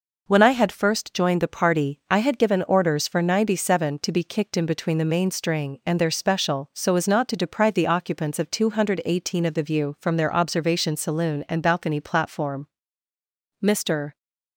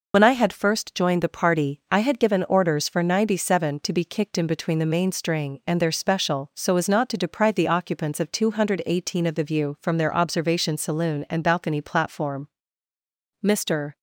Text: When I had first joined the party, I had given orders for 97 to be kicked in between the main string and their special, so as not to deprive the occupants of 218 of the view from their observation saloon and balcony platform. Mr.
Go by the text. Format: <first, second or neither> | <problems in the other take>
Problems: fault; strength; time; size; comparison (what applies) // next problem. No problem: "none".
first | loses the start of "When"; at 0.1 s; 65 ms